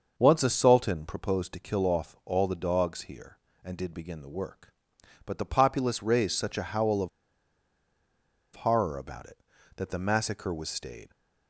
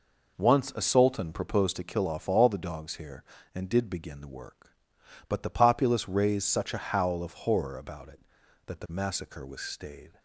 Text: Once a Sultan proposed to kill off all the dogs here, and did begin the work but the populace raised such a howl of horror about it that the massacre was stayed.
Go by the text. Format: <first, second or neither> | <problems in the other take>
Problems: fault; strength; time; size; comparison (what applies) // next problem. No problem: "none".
second | starts louder than the rest; until 1.1 s; 6.5 dB // pauses between "of" and "horror"; strong; at 7.0 s; 1.4 s long